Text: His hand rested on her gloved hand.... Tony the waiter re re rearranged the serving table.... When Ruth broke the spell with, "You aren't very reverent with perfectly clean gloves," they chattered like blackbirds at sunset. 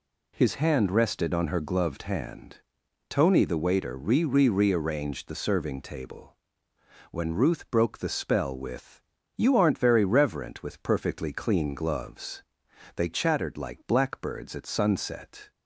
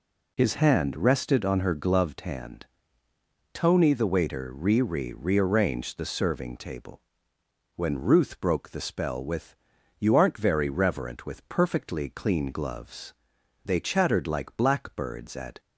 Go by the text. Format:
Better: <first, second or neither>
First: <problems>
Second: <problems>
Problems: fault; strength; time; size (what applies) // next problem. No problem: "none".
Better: first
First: none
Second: stops before "sunset"; at 15.5 s